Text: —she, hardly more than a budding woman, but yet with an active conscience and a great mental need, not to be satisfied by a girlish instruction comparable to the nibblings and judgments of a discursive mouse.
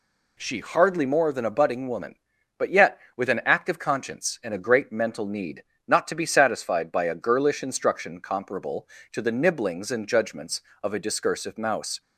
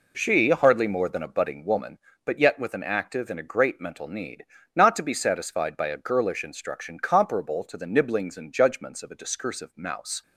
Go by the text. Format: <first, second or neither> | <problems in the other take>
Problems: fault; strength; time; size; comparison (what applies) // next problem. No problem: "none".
first | skips "conscience"; at 3.2 s